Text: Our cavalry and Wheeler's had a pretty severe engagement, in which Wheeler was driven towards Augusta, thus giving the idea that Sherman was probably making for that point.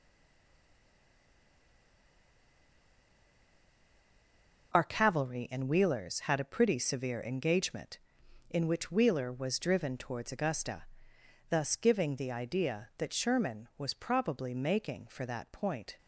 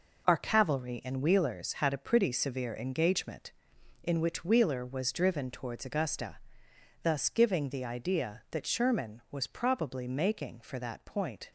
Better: second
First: stays silent before the first word; strong; until 4.7 s; 4.7 s long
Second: none

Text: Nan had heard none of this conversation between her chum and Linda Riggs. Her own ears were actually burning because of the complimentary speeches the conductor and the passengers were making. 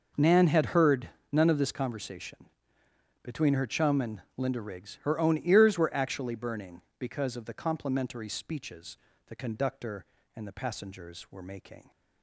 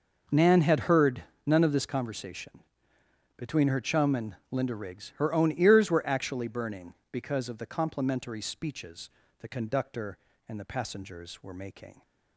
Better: neither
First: pauses between "heard" and "none"; slight; at 1.0 s; 0.22 s long // pauses between "conversation" and "between"; noticeable; at 2.4 s; 0.78 s long // pauses between "and" and "Linda"; slight; at 4.2 s; 0.16 s long // pauses between "speeches" and "the"; slight; at 8.9 s; 0.30 s long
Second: pauses between "heard" and "none"; slight; at 1.2 s; 0.22 s long // pauses between "conversation" and "between"; noticeable; at 2.5 s; 0.78 s long // pauses between "and" and "Linda"; slight; at 4.3 s; 0.16 s long // pauses between "speeches" and "the"; slight; at 9.0 s; 0.30 s long

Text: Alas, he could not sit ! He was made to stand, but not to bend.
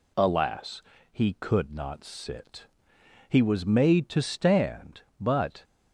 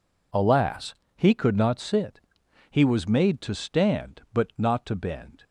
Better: second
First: stops before "not to bend"; at 5.6 s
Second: none

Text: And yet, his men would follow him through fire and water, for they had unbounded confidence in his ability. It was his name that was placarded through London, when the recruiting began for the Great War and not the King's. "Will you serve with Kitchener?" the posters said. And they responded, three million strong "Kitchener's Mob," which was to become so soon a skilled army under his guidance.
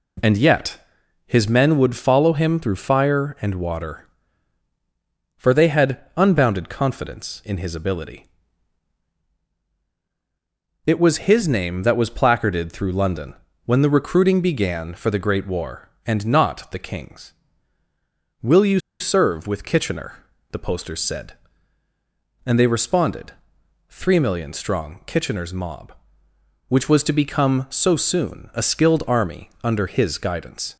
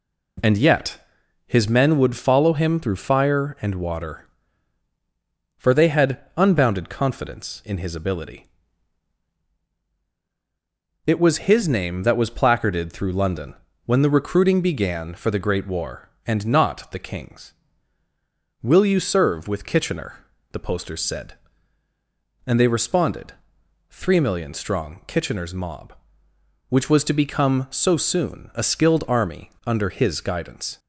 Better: second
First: pauses between "had" and "unbounded"; slight; at 6.0 s; 0.16 s long // pauses between "you" and "serve"; slight; at 18.8 s; 0.19 s long // pauses between "army" and "under"; slight; at 29.4 s; 0.16 s long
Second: pauses between "had" and "unbounded"; slight; at 6.2 s; 0.16 s long // pauses between "army" and "under"; slight; at 29.4 s; 0.18 s long

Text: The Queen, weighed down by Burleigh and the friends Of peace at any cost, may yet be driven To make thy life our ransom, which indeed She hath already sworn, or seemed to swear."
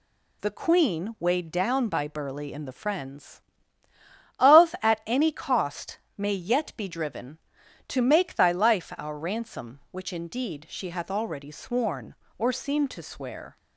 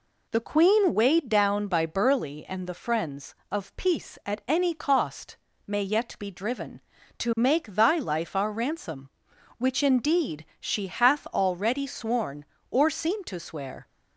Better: second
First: skips "peace"; at 4.7 s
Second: none

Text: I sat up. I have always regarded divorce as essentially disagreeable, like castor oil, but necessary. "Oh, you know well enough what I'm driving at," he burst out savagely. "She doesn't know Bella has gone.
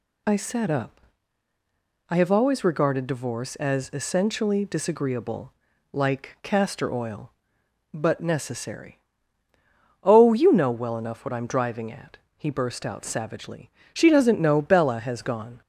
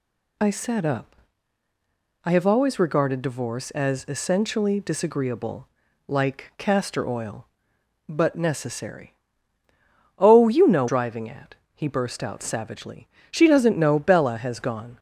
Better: first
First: none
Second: skips "well enough what I'm"; at 10.8 s

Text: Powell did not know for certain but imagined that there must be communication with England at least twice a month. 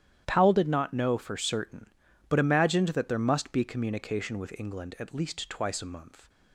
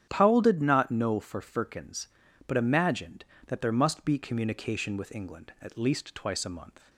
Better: first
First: starts louder than the rest; strong; until 1.2 s; 11 dB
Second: starts louder than the rest; strong; until 1.1 s; 9.5 dB // says "firkins" for "certain"; at 1.4 s

